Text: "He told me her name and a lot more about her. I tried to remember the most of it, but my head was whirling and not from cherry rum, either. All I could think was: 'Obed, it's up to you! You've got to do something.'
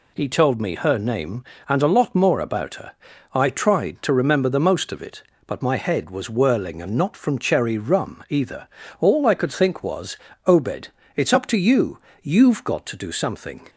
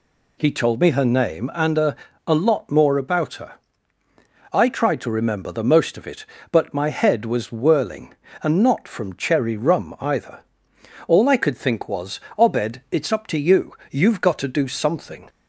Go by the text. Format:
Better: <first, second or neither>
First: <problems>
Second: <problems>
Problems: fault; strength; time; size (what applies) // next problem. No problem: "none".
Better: first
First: none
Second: says "a" twice; at 2.2 s